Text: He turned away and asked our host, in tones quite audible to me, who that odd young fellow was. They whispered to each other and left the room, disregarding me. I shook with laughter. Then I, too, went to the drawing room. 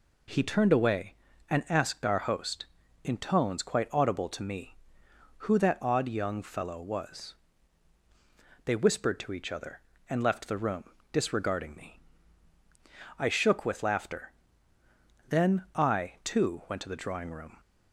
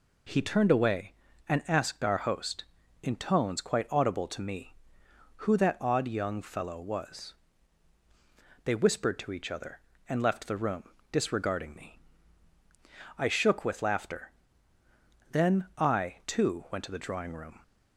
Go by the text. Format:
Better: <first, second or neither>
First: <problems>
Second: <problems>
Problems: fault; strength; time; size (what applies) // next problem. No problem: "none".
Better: neither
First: none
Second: none